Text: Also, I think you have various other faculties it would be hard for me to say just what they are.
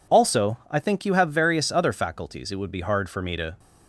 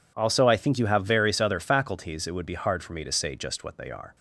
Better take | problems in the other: second | stops before "say just what they are"; at 3.5 s

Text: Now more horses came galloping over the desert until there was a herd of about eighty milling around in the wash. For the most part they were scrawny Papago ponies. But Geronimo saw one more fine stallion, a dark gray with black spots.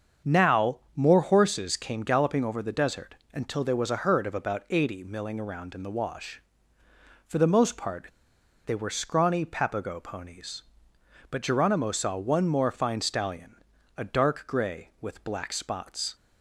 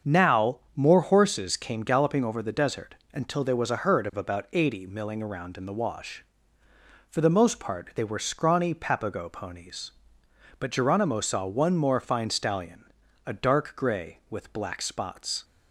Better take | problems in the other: second | starts louder than the rest; strong; until 1.4 s; 7 dB; strong in the second // pauses between "Now" and "more"; slight; at 0.7 s; 0.18 s long; slight in the second // pauses between "desert" and "until"; slight; at 3.1 s; 0.18 s long; slight in the second // pauses between "part" and "they"; noticeable; at 8.0 s; 0.57 s long

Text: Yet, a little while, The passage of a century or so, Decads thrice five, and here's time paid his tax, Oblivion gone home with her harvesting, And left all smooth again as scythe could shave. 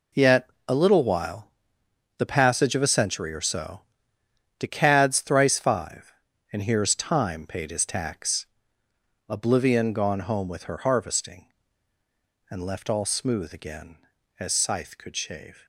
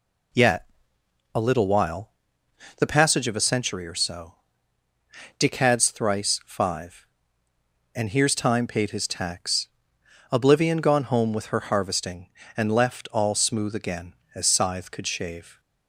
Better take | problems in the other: neither | none

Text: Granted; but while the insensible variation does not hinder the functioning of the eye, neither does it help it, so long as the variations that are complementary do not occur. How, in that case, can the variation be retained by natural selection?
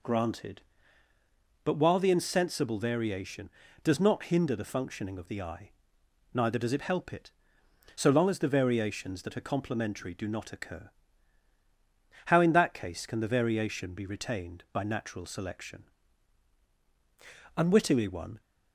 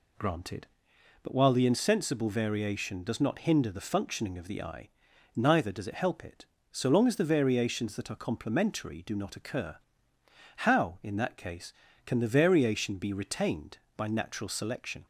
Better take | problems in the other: second | goes on to say "Unwittingly one"; noticeable; from 17.5 s on; 0.84 s long

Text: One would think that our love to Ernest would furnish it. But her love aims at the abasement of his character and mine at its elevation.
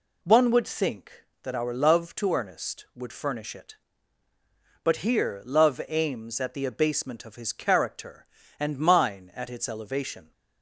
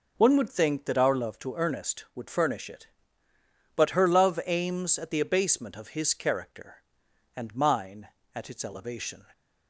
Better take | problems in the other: second | says "here" for "her"; at 4.9 s

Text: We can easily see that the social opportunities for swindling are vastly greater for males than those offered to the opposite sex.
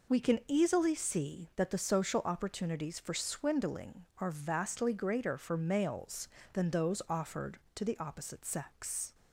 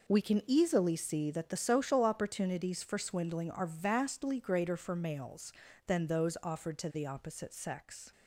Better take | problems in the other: neither | none

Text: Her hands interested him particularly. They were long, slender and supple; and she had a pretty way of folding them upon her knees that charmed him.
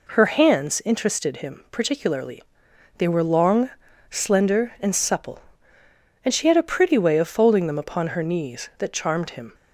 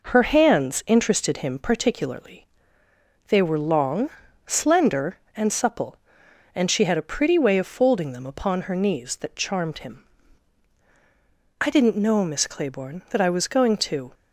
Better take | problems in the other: first | goes on to say "I didn't know Miss Claiborne that I was going to"; strong; from 11.6 s on; 2.5 s long

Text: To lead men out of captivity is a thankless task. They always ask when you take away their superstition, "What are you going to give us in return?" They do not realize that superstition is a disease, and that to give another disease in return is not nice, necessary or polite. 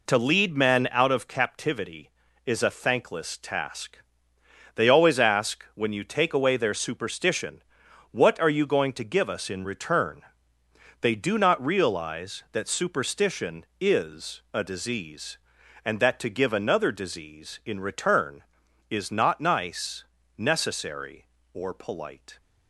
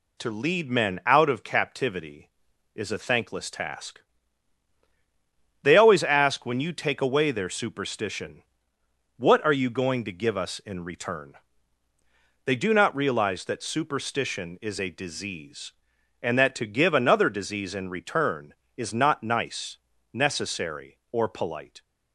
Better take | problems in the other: neither | none

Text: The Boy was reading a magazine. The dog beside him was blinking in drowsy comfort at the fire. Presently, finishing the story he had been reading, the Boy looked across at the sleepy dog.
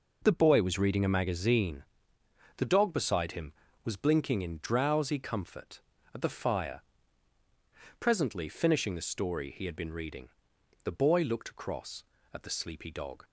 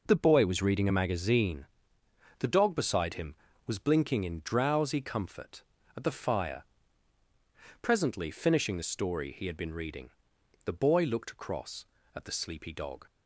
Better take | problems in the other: neither | none

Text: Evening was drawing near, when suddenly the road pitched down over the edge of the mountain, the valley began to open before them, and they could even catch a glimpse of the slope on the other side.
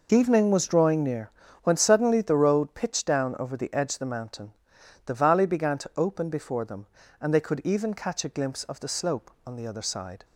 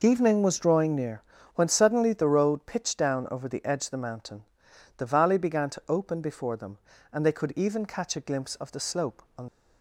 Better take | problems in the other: first | stops before "the other side"; at 9.4 s

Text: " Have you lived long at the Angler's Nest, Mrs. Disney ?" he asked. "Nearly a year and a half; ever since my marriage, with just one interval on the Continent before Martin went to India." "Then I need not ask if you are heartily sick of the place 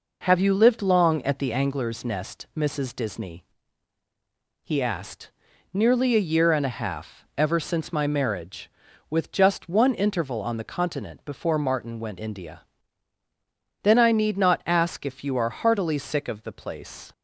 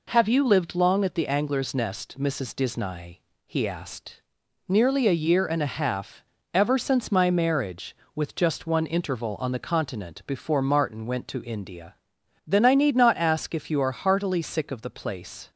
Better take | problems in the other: second | skips "to"; at 12.1 s

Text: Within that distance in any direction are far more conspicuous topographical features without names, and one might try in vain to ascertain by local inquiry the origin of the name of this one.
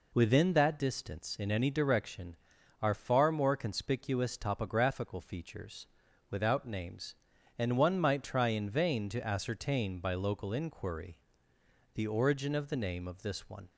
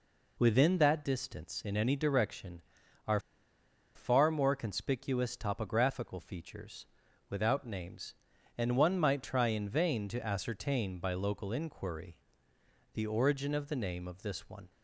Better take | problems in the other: first | pauses between "are" and "far"; noticeable; at 3.1 s; 0.76 s long // pauses between "features" and "without"; at 6.8 s; 0.42 s long; also in the first // pauses between "inquiry" and "the"; noticeable; at 12.1 s; 0.78 s long; noticeable in the first

